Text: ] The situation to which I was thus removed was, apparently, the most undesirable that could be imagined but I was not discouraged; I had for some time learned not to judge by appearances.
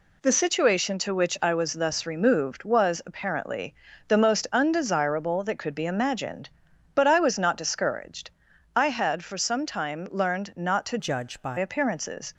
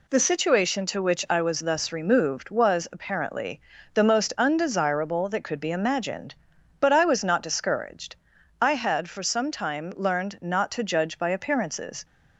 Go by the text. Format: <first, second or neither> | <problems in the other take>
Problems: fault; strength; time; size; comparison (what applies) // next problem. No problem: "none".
second | changes voice from "judge" to "by"; from 10.9 to 11.5 s; 0.6 s long